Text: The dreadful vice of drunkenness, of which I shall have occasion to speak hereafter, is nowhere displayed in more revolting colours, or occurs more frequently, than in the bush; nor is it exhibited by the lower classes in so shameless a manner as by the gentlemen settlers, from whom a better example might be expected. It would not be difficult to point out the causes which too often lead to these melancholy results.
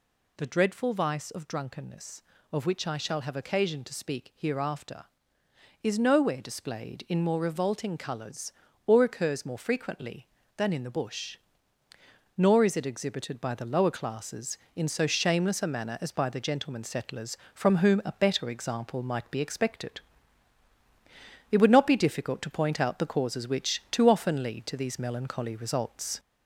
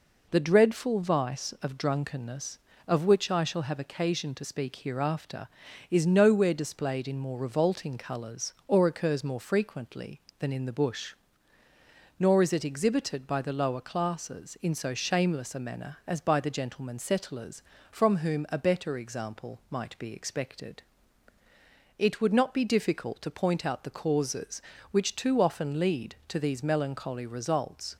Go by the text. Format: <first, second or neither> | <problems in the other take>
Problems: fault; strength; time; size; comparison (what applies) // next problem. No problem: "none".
second | gets louder; slight; throughout; 2.5 dB